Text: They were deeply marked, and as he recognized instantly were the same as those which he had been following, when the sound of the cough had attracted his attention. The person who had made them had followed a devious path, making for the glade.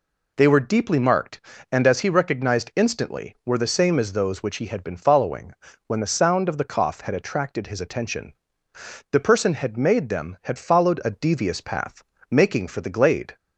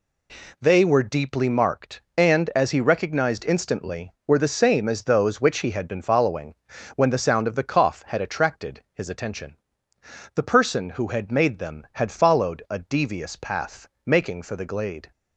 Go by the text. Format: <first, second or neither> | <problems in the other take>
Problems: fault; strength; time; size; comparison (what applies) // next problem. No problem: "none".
second | skips "who"; at 9.5 s